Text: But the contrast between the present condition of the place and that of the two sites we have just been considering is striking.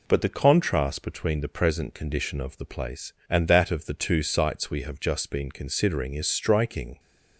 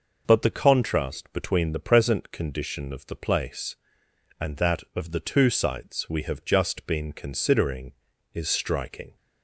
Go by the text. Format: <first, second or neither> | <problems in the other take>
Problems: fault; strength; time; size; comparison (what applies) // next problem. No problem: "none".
neither | none